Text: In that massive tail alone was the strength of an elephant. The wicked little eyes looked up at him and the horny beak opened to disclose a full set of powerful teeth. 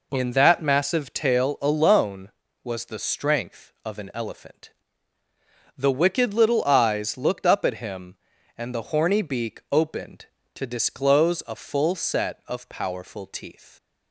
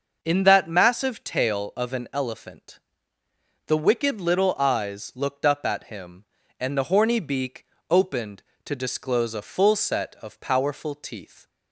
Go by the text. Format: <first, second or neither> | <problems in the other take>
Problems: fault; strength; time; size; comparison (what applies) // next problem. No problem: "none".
first | skips "alone was the strength"; at 1.7 s // pauses between "beak" and "opened"; slight; at 7.6 s; 0.24 s long